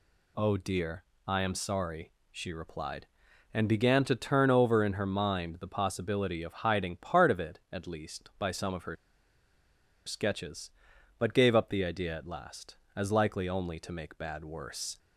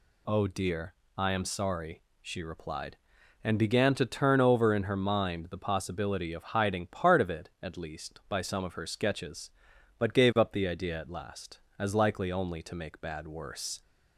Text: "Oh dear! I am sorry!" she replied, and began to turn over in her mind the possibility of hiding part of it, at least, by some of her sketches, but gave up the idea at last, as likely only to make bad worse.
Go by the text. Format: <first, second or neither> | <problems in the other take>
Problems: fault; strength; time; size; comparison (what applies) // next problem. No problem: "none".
second | pauses between "her" and "sketches"; at 8.9 s; 1.1 s long